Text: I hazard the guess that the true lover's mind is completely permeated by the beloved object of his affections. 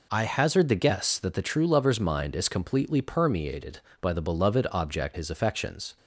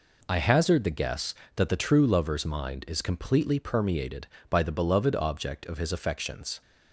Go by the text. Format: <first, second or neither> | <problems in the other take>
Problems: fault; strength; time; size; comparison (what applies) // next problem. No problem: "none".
second | skips "of"; at 5.1 s